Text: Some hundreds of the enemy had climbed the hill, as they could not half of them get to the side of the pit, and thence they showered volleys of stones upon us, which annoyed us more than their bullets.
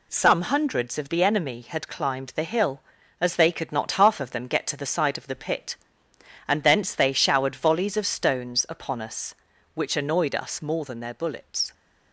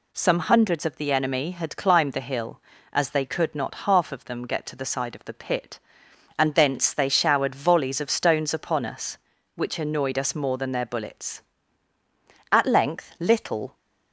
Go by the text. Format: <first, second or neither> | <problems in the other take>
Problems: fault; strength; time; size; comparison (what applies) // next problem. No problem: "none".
first | goes on to say "At length Little"; noticeable; from 12.5 s on; 1.2 s long